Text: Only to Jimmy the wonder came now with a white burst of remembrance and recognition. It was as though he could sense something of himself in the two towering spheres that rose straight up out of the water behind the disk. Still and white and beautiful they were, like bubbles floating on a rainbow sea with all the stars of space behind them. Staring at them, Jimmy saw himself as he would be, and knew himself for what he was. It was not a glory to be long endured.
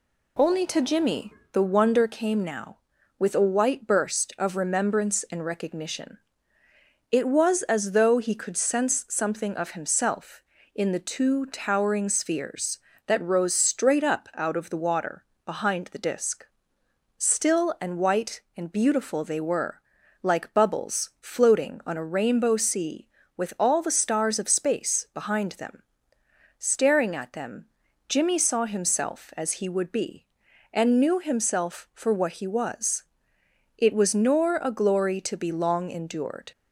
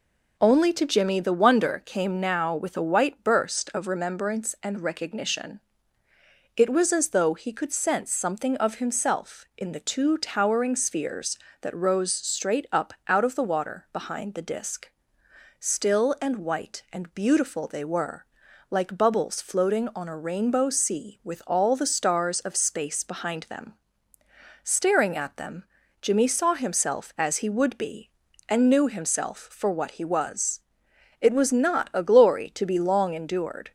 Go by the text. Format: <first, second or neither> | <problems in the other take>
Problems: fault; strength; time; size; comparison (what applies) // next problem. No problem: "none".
second | pauses between "Jimmy" and "the"; slight; at 1.3 s; 0.18 s long // pauses between "water" and "behind"; slight; at 15.2 s; 0.18 s long // says "nor" for "not"; at 34.1 s